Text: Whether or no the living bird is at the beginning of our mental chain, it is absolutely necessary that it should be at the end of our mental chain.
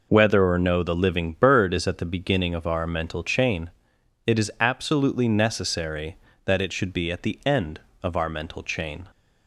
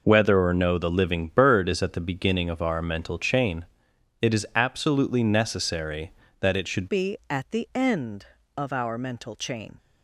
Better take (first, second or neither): first